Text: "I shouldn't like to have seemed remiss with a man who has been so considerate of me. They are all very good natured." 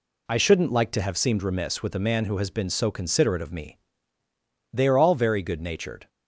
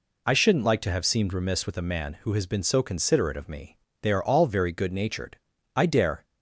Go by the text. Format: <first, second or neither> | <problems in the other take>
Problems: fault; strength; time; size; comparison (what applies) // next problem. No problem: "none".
first | goes on to say "I dare"; slight; from 5.7 s on; 0.48 s long